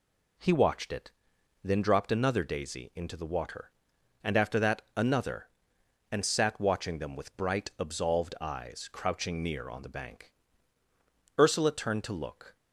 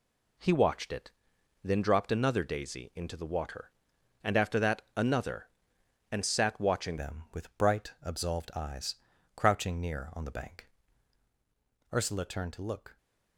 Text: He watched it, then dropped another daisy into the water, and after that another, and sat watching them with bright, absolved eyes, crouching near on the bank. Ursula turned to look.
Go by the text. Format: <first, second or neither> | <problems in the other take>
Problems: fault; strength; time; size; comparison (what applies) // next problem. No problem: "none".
first | changes voice at "them"; from 6.9 s on; 6.0 s long